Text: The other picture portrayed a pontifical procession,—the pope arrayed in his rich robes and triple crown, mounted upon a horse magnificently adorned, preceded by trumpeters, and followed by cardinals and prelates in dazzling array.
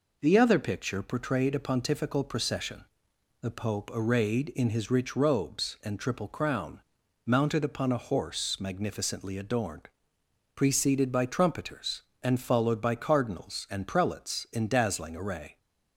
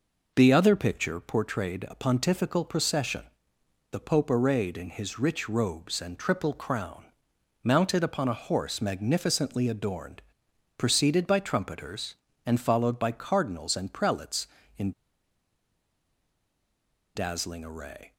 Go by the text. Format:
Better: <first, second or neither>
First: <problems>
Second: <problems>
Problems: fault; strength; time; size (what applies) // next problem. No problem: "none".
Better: first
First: none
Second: pauses between "in" and "dazzling"; strong; at 14.9 s; 2.2 s long